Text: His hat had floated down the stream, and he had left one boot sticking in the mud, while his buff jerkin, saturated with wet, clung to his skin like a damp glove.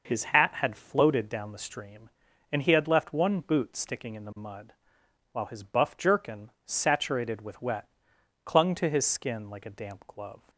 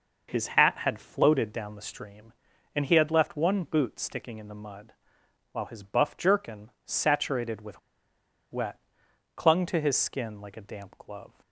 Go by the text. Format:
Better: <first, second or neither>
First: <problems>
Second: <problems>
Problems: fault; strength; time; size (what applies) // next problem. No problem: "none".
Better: first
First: none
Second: pauses between "with" and "wet"; noticeable; at 7.7 s; 0.72 s long